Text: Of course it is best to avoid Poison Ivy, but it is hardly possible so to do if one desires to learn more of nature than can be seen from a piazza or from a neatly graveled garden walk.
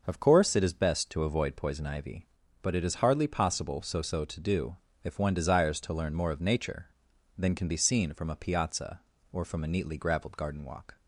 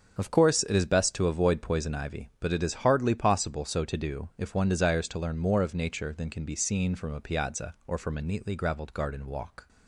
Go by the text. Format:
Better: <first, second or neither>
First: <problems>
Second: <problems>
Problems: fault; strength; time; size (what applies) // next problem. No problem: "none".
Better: second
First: starts louder than the rest; noticeable; until 1.0 s; 6 dB // says "so" twice; at 4.0 s // pauses between "do" and "if"; slight; at 4.7 s; 0.26 s long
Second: starts louder than the rest; until 1.2 s; 7 dB